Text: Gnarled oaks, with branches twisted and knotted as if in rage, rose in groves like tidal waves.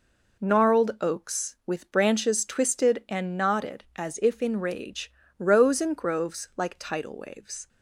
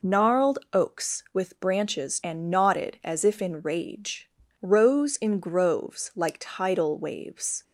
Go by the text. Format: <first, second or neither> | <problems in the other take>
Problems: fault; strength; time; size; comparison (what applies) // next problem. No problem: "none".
first | pauses between "Gnarled" and "oaks"; slight; at 0.5 s; 0.16 s long // skips "twisted"; at 2.2 s